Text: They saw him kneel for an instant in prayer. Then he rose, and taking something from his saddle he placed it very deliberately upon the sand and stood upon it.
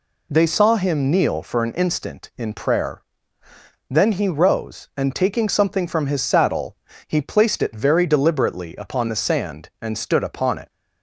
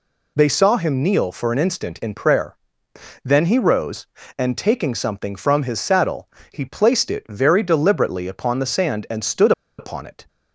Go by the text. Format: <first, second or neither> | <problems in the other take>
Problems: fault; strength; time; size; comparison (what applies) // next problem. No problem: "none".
first | pauses between "saddle" and "he"; slight; at 6.2 s; 0.24 s long; slight in the first // pauses between "stood" and "upon"; slight; at 9.5 s; 0.26 s long